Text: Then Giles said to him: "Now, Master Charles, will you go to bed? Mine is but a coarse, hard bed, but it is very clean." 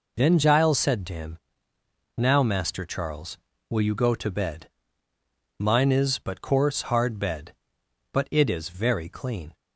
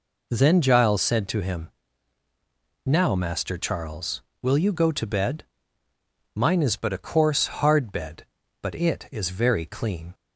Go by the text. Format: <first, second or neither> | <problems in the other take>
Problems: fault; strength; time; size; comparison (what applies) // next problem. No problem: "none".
second | skips "a"; at 6.3 s